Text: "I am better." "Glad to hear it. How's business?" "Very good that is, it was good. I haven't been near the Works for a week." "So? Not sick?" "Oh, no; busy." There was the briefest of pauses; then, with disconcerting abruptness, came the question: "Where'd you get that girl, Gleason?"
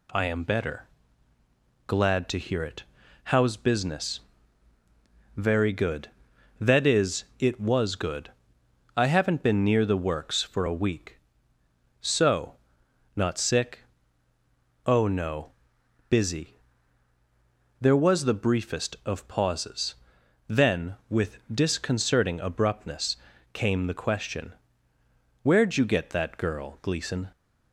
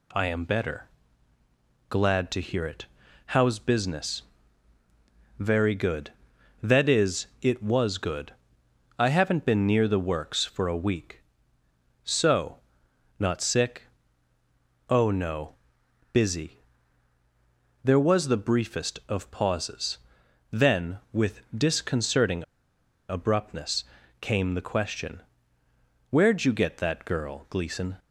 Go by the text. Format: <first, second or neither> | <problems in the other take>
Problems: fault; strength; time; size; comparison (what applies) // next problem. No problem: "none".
first | pauses between "with" and "disconcerting"; slight; at 21.4 s; 0.16 s long; slight in the first // pauses between "disconcerting" and "abruptness"; noticeable; at 22.4 s; 0.65 s long